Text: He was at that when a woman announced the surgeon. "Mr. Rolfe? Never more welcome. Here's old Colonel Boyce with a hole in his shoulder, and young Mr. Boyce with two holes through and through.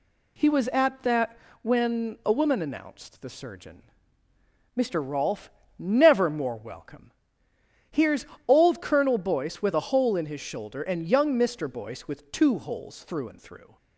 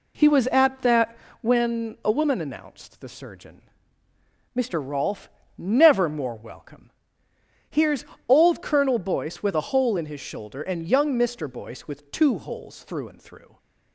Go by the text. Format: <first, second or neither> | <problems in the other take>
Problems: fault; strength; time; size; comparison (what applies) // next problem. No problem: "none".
first | starts louder than the rest; slight; until 1.7 s; 3 dB // pauses between "that" and "when"; slight; at 1.1 s; 0.28 s long; slight in the first // pauses between "Here's" and "old"; slight; at 8.0 s; 0.20 s long; slight in the first